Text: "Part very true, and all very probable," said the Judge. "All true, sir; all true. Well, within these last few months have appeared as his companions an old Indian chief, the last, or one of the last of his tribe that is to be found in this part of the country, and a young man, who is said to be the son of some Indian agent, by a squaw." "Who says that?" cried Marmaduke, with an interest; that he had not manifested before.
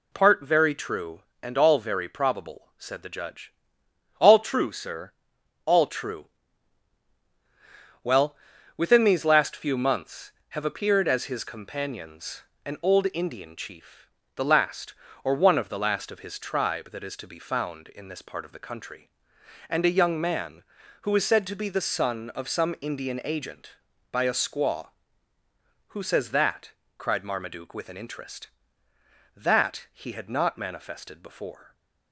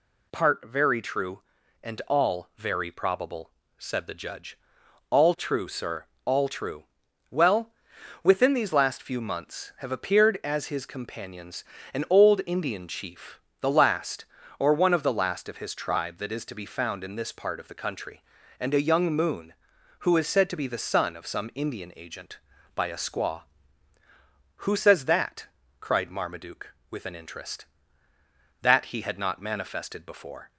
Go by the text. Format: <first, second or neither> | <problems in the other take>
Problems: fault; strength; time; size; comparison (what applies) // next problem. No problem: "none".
first | pauses between "companions" and "an"; slight; at 11.6 s; 0.32 s long; slight in the first // says "moon" for "man"; at 19.1 s